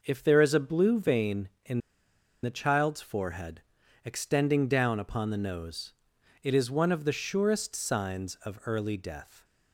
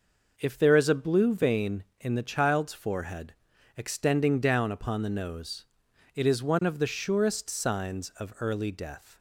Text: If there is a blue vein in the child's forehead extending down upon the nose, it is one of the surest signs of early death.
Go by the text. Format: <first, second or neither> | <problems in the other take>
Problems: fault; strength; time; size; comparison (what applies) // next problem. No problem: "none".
second | pauses between "in" and "the"; noticeable; at 1.7 s; 0.64 s long // pauses between "forehead" and "extending"; noticeable; at 3.5 s; 0.46 s long; noticeable in the second